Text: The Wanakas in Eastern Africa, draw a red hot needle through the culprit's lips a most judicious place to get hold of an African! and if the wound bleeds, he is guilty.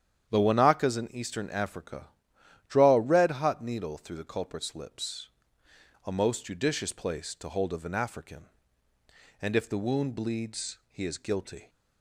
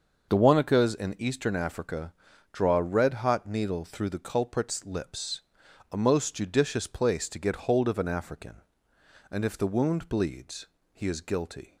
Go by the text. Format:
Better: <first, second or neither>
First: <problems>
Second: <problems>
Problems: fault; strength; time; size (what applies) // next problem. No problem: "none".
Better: second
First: starts louder than the rest; strong; until 1.3 s; 9 dB // pauses between "lips" and "a"; noticeable; at 5.2 s; 0.76 s long // skips "get"; at 7.4 s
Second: starts louder than the rest; until 1.3 s; 6 dB // pauses between "lips" and "a"; noticeable; at 5.4 s; 0.50 s long